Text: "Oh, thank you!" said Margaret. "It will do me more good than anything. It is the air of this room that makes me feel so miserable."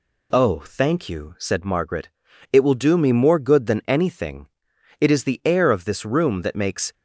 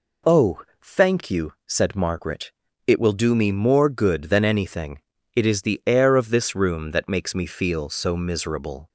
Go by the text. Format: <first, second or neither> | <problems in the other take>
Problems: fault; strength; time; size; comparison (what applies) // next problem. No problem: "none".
second | stops before "me feel so miserable"; at 6.9 s